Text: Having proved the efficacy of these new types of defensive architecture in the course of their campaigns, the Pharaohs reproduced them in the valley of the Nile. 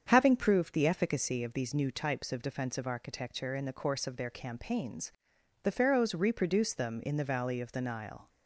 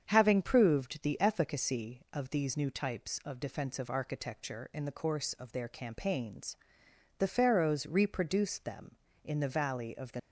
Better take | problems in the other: first | starts louder than the rest; strong; until 1.0 s; 7.5 dB; strong in the first // stops before "Nile"; at 10.1 s

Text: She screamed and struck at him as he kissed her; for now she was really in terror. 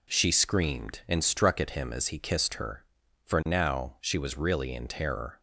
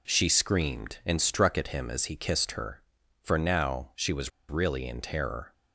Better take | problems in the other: first | pauses between "was" and "really"; slight; at 4.3 s; 0.18 s long

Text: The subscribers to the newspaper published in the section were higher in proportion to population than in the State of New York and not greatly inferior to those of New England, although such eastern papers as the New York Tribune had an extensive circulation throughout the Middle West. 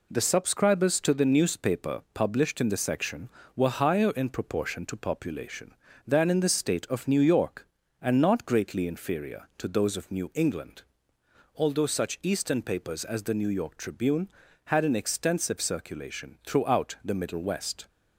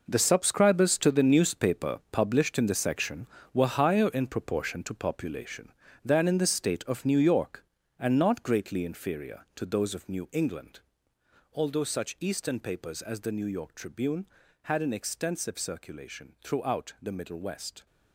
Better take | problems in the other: first | gets quieter; strong; throughout; 11.5 dB

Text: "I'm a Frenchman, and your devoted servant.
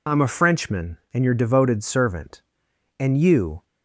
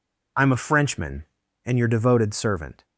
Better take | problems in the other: second | goes on to say "And you"; noticeable; from 2.9 s on; 0.66 s long

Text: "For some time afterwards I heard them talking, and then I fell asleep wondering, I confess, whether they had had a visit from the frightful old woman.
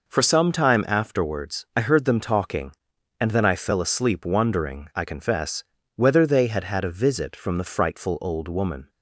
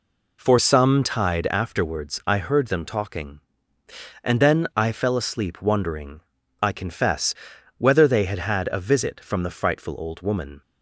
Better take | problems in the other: first | says "tide" for "time"; at 1.0 s

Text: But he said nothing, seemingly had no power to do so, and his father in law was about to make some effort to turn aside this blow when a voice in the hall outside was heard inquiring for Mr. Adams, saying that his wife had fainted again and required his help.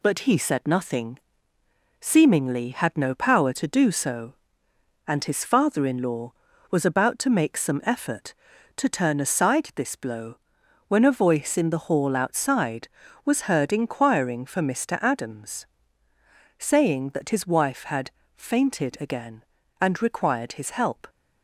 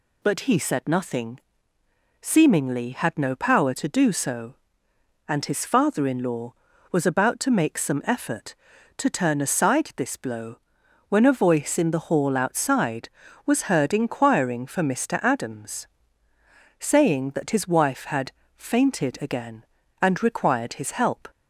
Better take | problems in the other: second | gets quieter; noticeable; throughout; 4 dB // pauses between "blow" and "when"; noticeable; at 10.3 s; 0.50 s long; noticeable in the second // pauses between "had" and "fainted"; slight; at 18.0 s; 0.24 s long; slight in the second

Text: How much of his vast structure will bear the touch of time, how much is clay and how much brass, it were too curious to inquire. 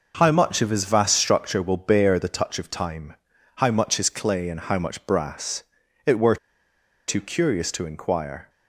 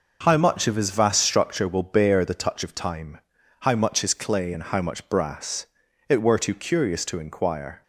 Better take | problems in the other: second | pauses between "were" and "too"; noticeable; at 6.3 s; 0.72 s long

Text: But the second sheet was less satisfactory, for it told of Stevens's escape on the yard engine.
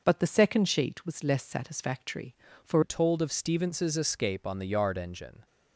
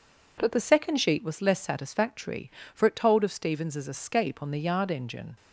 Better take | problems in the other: second | changes voice at "it"; from 2.8 s on; 2.6 s long

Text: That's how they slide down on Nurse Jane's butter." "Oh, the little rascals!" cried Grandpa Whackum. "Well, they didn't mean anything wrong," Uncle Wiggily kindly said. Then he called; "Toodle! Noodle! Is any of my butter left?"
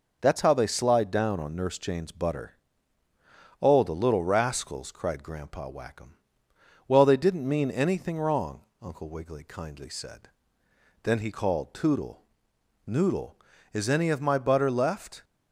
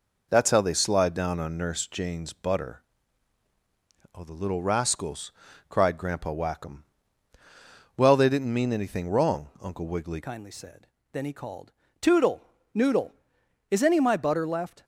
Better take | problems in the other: first | changes voice at "kindly"; from 10.2 s on; 4.6 s long

